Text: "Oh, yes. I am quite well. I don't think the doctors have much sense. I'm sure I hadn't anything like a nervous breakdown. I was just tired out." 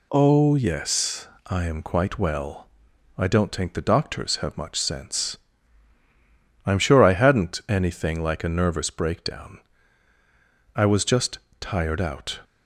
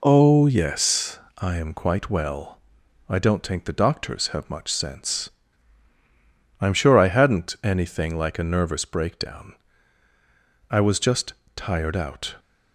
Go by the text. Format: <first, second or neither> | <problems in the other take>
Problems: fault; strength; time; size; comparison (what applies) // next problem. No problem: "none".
first | starts louder than the rest; until 1.3 s; 3.5 dB // pauses between "just" and "tired"; slight; at 11.3 s; 0.20 s long; slight in the first